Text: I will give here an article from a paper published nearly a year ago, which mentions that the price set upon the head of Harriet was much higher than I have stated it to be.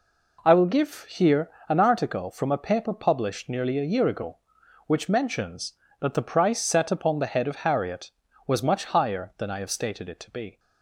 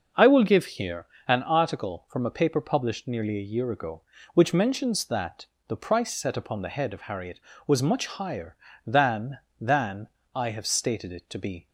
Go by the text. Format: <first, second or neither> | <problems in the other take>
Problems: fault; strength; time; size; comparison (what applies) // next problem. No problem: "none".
first | pauses between "here" and "an"; slight; at 1.0 s; 0.22 s long; slight in the first // pauses between "that" and "the"; slight; at 5.4 s; 0.22 s long // says "than" twice; at 9.6 s